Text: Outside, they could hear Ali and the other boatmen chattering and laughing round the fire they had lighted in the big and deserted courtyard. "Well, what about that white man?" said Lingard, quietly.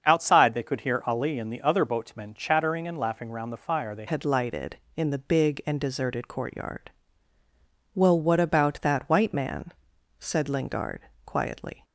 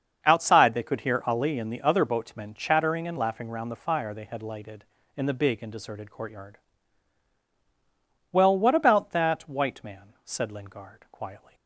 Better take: second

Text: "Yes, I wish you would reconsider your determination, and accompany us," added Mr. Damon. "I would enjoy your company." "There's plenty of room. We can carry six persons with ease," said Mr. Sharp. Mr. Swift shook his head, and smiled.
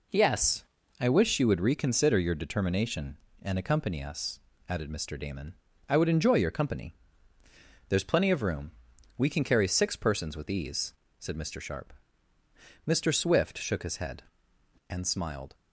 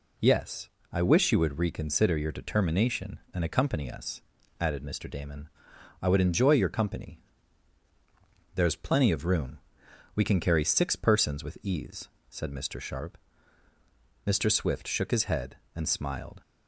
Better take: neither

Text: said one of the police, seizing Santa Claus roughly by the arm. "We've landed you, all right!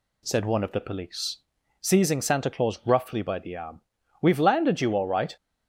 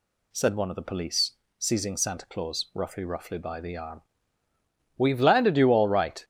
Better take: first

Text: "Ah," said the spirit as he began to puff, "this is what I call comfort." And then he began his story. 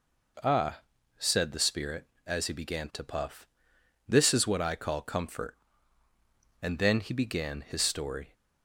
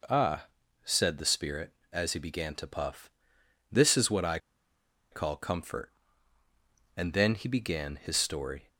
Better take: first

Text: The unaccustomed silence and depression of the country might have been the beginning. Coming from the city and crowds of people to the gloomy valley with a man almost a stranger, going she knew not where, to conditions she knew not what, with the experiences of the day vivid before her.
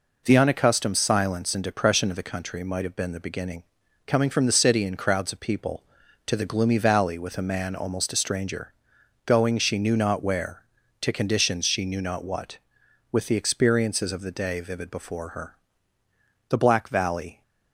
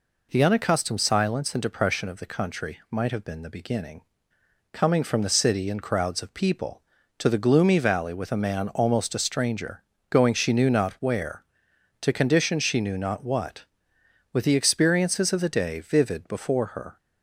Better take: second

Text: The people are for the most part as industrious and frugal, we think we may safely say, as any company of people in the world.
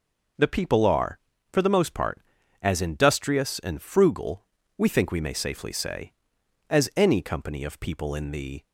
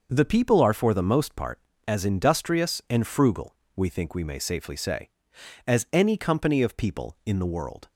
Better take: second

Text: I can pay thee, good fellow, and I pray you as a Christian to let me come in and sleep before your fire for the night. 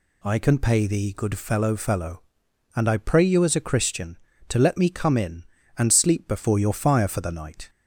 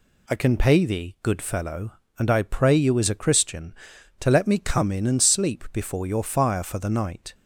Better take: second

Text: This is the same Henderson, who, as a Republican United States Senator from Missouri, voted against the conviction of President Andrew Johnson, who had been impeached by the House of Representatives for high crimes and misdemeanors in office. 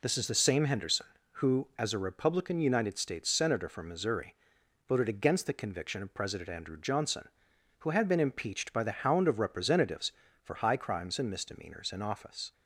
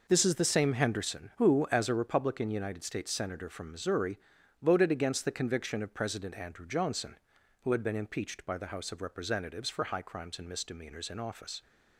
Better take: second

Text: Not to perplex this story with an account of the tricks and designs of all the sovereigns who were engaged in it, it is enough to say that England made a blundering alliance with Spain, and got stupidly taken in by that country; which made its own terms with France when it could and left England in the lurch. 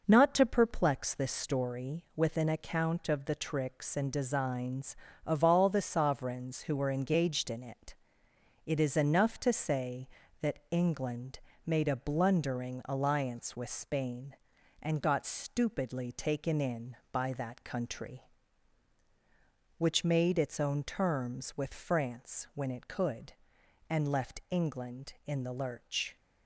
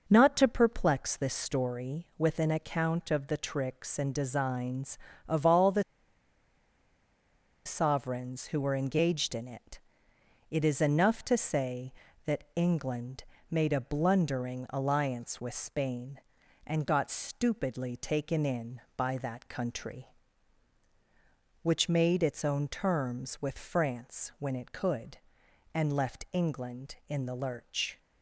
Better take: first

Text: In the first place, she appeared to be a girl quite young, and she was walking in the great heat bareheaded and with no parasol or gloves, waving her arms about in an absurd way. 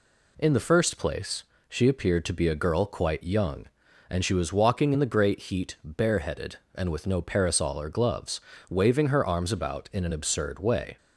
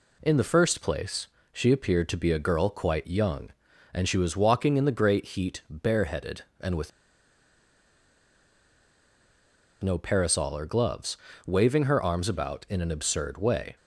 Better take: first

